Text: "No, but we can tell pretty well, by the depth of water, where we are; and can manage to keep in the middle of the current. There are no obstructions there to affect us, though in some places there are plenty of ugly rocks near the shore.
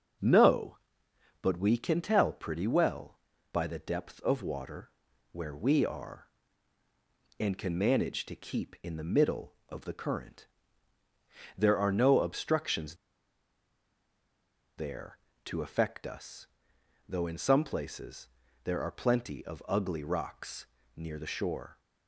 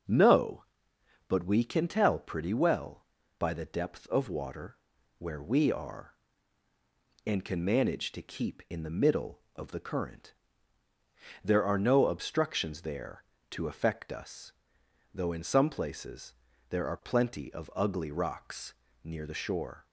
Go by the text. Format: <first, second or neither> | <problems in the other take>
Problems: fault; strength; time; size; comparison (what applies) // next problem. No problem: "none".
second | starts louder than the rest; strong; until 1.8 s; 7 dB; strong in the second // pauses between "obstructions" and "there"; strong; at 12.9 s; 1.8 s long // pauses between "places" and "there"; slight; at 18.2 s; 0.34 s long; slight in the second // pauses between "rocks" and "near"; slight; at 20.6 s; 0.28 s long; slight in the second